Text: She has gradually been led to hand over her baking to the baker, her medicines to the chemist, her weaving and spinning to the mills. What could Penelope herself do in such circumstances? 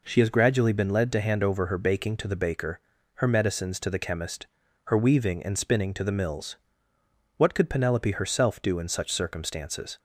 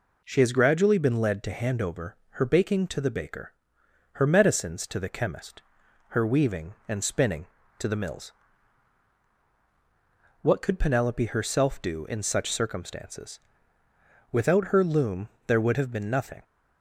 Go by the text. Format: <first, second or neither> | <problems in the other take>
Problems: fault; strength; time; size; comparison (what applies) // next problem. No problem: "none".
first | pauses between "over" and "her"; slight; at 2.1 s; 0.22 s long // goes on to say "Without her loom there would have been nothing"; strong; from 14.3 s on; 2.1 s long